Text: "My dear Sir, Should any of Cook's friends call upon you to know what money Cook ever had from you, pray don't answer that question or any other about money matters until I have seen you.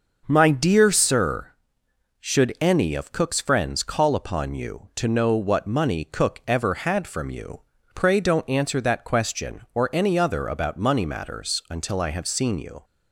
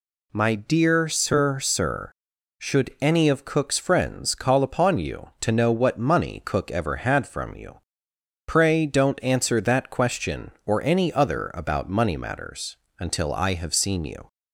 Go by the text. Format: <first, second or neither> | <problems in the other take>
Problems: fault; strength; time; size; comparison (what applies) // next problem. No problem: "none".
first | says "Sir" twice; at 1.5 s // pauses between "matters" and "until"; slight; at 12.7 s; 0.24 s long